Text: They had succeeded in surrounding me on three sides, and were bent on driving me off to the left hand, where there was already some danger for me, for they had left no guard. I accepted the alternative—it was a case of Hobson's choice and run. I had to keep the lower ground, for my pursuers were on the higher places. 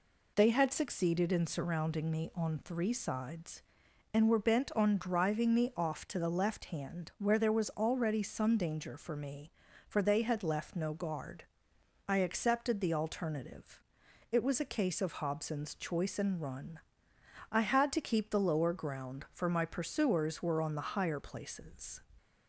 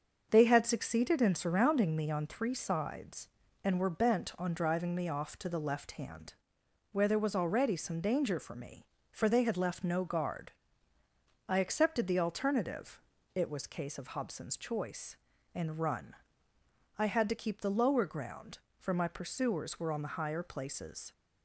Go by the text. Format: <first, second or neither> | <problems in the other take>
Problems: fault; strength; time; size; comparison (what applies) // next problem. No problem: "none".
first | starts louder than the rest; until 1.3 s; 6.5 dB // skips "a"; at 13.6 s